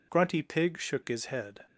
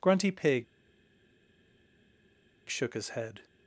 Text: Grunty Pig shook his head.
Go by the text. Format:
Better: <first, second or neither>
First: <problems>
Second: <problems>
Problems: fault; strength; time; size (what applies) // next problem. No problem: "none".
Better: first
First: none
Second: pauses between "Pig" and "shook"; strong; at 0.6 s; 2.0 s long